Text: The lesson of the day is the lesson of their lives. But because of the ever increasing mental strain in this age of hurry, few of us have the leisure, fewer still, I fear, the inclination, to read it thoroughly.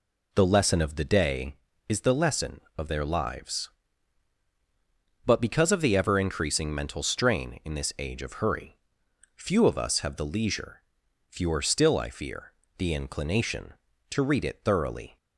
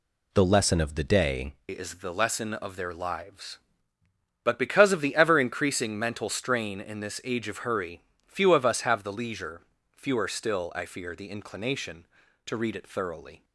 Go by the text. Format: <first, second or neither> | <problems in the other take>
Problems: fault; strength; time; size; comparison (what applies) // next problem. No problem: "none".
first | changes voice at "is"; from 1.7 s on; 11.7 s long